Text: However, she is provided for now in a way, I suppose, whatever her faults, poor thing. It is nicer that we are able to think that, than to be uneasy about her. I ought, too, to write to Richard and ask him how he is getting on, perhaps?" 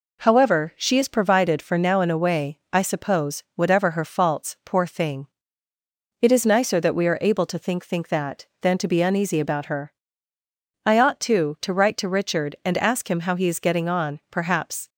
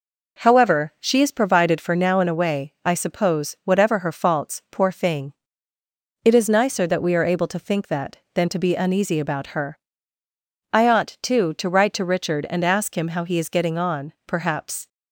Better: second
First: says "think" twice; at 7.8 s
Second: none

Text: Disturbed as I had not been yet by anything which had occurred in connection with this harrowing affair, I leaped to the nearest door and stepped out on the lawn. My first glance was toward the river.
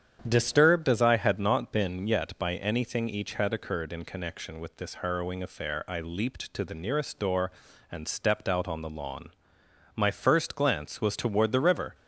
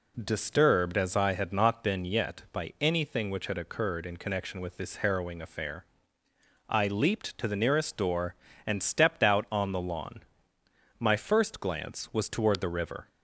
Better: second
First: starts louder than the rest; strong; until 1.2 s; 9 dB // says "each" for "which"; at 3.0 s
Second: none

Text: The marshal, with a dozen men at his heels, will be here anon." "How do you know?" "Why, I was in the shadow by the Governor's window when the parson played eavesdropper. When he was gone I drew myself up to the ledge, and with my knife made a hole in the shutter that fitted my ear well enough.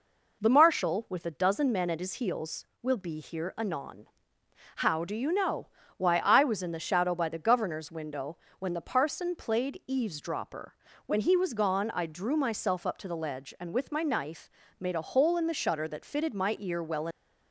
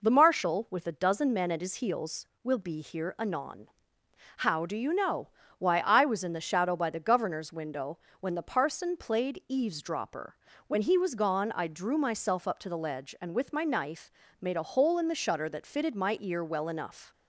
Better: second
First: pauses between "window" and "when"; slight; at 8.3 s; 0.22 s long // pauses between "knife" and "made"; slight; at 14.4 s; 0.30 s long // stops before "enough"; at 17.1 s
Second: pauses between "window" and "when"; slight; at 7.9 s; 0.22 s long // pauses between "knife" and "made"; slight; at 14.1 s; 0.30 s long

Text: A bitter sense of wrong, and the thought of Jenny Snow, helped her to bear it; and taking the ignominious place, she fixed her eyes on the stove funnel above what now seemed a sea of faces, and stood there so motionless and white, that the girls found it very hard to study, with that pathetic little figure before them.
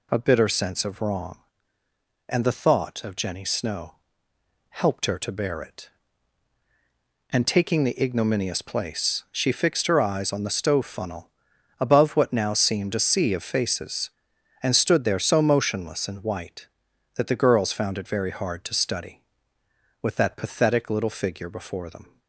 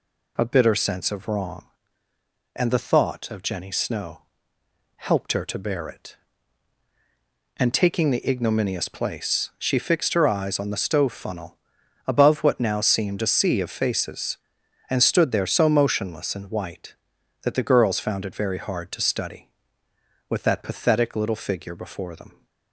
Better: neither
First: pauses between "funnel" and "above"; noticeable; at 11.2 s; 0.50 s long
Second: pauses between "funnel" and "above"; noticeable; at 11.5 s; 0.50 s long

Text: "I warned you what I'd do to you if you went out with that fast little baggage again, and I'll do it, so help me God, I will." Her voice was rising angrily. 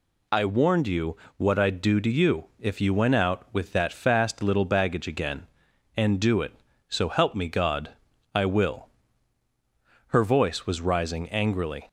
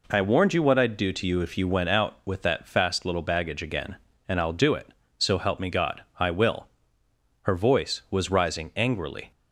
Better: second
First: pauses between "you" and "what"; slight; at 1.1 s; 0.22 s long // skips "I'll"; at 6.1 s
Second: none

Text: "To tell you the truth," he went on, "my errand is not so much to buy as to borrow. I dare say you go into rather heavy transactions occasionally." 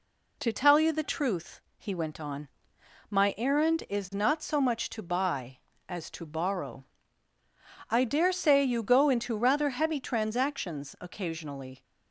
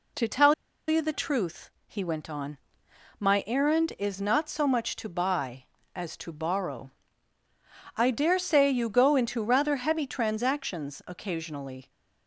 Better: first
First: none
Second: pauses between "tell" and "you"; slight; at 0.5 s; 0.34 s long

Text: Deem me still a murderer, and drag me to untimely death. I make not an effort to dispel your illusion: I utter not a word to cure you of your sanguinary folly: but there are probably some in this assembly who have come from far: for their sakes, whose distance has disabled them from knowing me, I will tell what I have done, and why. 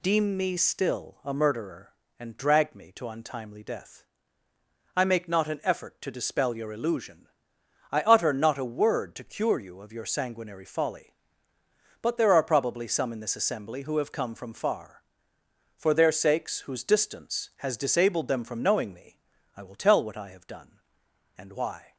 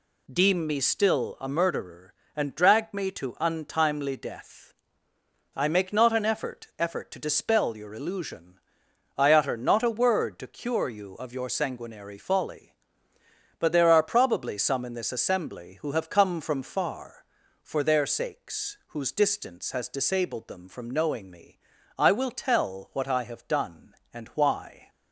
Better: first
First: none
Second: says "effort" twice; at 6.7 s

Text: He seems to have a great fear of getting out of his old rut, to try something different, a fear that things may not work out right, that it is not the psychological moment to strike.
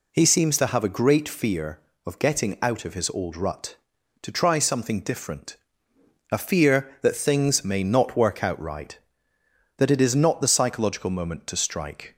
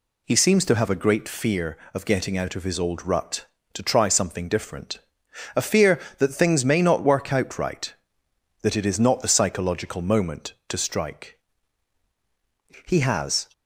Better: first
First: none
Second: goes on to say "He has"; from 12.8 s on; 0.60 s long

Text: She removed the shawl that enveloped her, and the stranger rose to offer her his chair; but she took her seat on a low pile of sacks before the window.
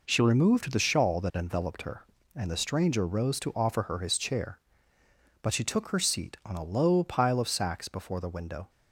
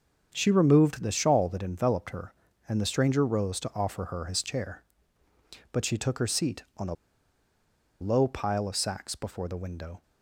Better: first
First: none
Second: starts louder than the rest; until 1.3 s; 7 dB // pauses between "a" and "low"; at 6.9 s; 1.0 s long

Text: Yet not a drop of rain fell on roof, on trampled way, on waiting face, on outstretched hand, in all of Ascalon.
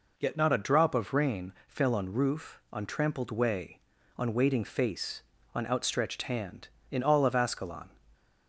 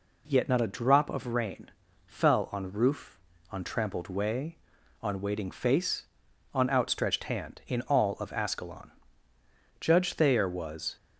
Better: first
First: pauses between "rain" and "fell"; slight; at 1.5 s; 0.16 s long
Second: pauses between "rain" and "fell"; slight; at 1.7 s; 0.36 s long // goes on to say "Judge Thayer was"; noticeable; from 9.8 s on; 1.1 s long

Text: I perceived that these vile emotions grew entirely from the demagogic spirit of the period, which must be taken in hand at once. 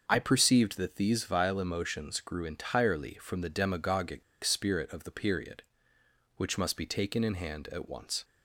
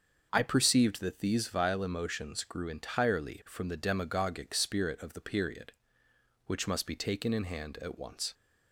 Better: second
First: starts louder than the rest; until 1.0 s; 6.5 dB // pauses between "demagogic" and "spirit"; slight; at 4.2 s; 0.22 s long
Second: starts louder than the rest; until 1.3 s; 6.5 dB

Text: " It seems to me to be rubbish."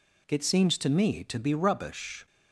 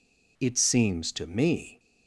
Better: first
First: none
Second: stops before "to be rubbish"; at 1.7 s

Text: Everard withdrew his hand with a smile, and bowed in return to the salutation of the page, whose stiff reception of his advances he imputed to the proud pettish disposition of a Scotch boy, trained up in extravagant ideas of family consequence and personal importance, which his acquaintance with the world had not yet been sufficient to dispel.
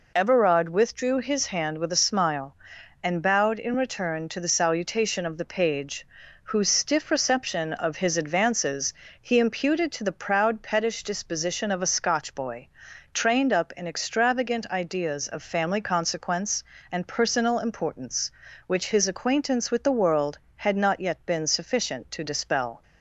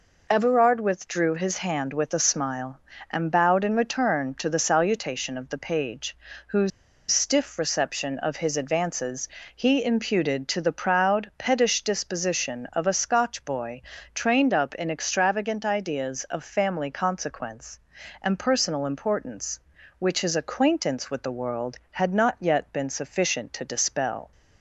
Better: first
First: pauses between "advances" and "he"; slight; at 8.9 s; 0.26 s long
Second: pauses between "whose" and "stiff"; at 6.7 s; 0.41 s long // pauses between "advances" and "he"; slight; at 9.2 s; 0.28 s long

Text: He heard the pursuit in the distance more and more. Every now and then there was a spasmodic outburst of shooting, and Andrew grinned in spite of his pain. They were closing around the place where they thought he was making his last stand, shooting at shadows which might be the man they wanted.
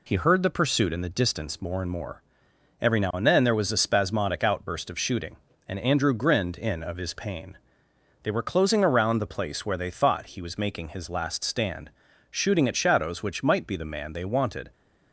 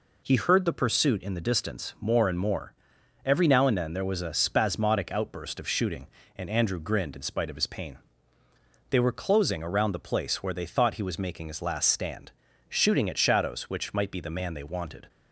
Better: second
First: skips "spite"; at 6.8 s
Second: none

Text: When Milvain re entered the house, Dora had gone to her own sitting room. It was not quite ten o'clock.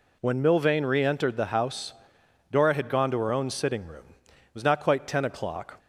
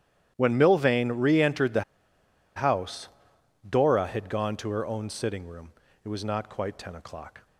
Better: first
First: none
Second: starts louder than the rest; strong; until 1.3 s; 11 dB // pauses between "the" and "house"; noticeable; at 1.8 s; 0.74 s long

